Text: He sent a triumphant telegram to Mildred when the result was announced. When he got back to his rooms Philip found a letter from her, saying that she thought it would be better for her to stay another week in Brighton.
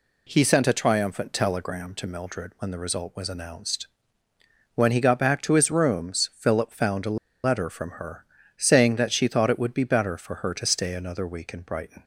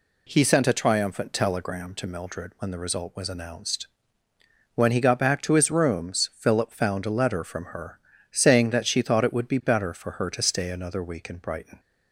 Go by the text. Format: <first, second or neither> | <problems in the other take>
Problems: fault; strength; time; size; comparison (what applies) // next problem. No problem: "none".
second | pauses between "a" and "letter"; slight; at 7.1 s; 0.27 s long